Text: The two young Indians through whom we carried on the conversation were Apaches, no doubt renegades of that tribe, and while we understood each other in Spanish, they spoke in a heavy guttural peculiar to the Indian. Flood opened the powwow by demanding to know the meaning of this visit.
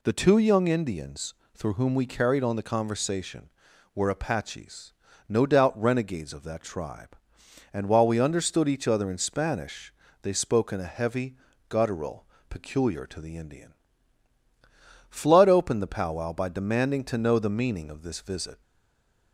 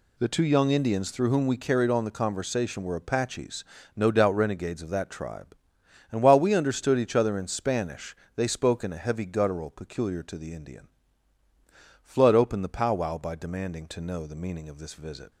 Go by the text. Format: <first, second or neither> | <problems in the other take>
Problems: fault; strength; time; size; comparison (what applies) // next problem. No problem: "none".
second | pauses between "Indians" and "through"; slight; at 1.3 s; 0.20 s long // pauses between "heavy" and "guttural"; slight; at 11.3 s; 0.34 s long // pauses between "guttural" and "peculiar"; slight; at 12.2 s; 0.24 s long // stays silent after the last word; slight; from 18.6 s on; 0.7 s long